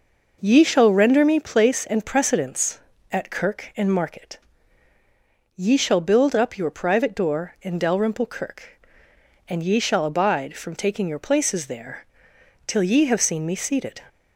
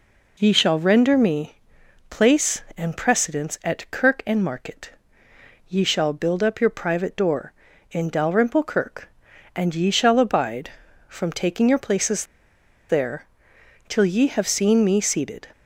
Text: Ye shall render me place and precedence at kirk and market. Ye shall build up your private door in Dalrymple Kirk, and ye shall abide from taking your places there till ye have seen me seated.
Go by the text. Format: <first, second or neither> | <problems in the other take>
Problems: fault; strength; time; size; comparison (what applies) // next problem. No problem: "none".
first | pauses between "me" and "place"; noticeable; at 1.5 s; 0.54 s long // pauses between "places" and "there"; noticeable; at 12.2 s; 0.64 s long // pauses between "there" and "till"; noticeable; at 13.2 s; 0.64 s long; noticeable in the first